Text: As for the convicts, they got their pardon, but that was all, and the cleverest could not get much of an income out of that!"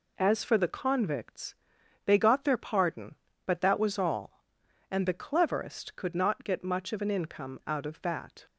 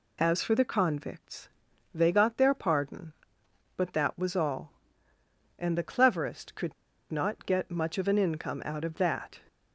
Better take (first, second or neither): first